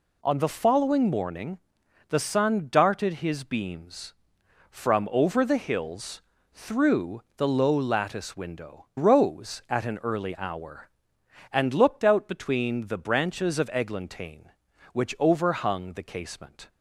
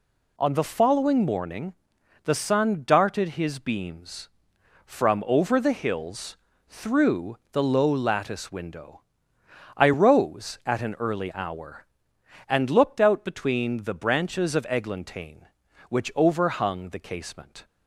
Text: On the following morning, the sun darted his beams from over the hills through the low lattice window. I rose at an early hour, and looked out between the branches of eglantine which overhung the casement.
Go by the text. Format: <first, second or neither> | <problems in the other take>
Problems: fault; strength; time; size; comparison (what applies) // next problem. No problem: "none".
second | pauses between "hills" and "through"; slight; at 6.2 s; 0.30 s long; slight in the second // skips "I"; at 8.9 s